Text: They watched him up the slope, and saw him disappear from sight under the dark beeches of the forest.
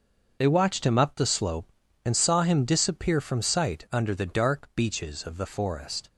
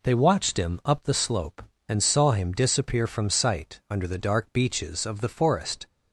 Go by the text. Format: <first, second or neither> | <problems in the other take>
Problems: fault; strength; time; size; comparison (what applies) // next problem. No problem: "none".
second | gets quieter; strong; throughout; 11.5 dB